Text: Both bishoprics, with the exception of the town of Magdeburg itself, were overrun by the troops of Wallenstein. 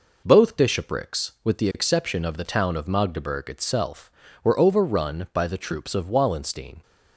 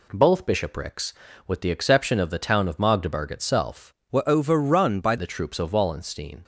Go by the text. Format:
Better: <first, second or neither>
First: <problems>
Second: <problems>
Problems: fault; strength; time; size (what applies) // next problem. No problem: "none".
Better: first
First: none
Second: changes voice from "were" to "by"; from 4.1 to 5.1 s; 1.0 s long